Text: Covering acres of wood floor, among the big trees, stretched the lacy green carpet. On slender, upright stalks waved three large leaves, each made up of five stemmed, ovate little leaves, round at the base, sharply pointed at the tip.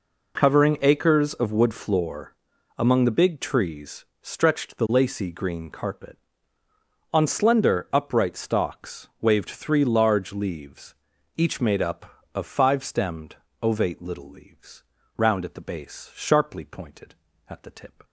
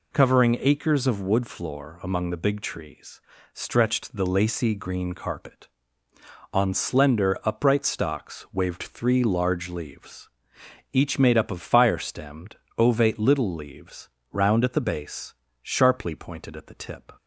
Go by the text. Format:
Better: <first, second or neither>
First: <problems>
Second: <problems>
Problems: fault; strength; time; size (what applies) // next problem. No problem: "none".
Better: first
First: none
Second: says "fire" for "five"; at 11.6 s